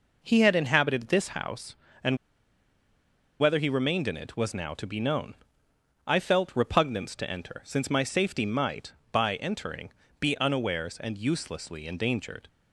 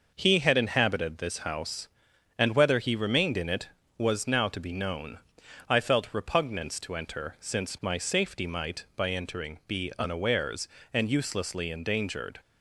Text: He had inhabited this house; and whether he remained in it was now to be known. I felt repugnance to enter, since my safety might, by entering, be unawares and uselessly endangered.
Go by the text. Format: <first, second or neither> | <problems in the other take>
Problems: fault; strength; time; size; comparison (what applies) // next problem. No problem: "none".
second | pauses between "and" and "whether"; at 2.1 s; 1.2 s long